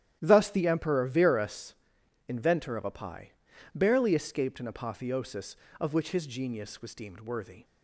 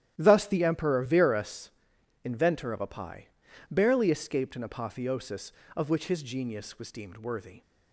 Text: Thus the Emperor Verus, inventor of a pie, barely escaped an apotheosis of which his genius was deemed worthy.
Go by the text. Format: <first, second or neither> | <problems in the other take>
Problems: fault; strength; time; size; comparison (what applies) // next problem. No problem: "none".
neither | starts louder than the rest; strong; the same in both